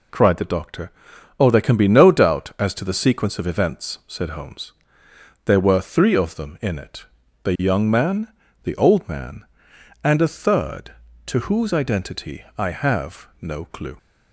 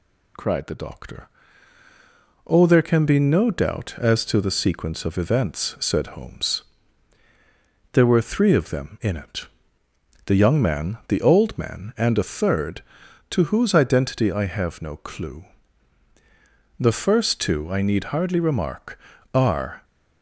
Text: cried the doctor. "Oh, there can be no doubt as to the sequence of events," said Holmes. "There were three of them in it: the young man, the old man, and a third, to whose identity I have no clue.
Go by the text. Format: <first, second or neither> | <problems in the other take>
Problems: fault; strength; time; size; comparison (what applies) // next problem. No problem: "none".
first | goes on to say "The first two I need hardly remark are"; strong; from 16.7 s on; 3.0 s long